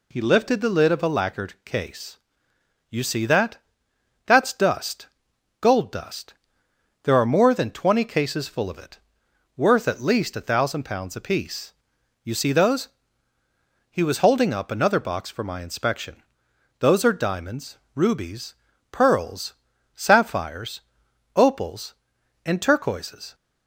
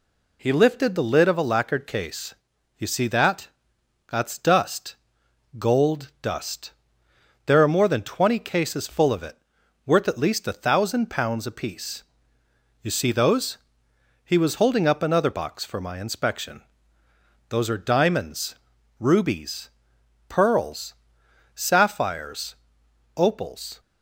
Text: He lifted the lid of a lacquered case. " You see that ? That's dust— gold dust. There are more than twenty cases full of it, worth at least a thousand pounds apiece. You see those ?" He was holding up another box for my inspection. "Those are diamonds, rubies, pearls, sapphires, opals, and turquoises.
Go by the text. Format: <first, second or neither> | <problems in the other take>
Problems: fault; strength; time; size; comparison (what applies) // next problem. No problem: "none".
first | stops before "and turquoises"; at 23.7 s